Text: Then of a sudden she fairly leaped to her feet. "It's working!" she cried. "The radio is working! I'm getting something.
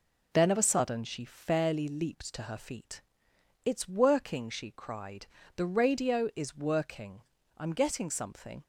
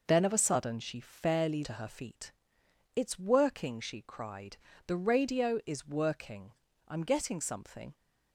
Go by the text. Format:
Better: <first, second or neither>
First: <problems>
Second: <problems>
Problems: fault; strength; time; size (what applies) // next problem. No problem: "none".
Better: first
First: none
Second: skips "leaped"; at 1.6 s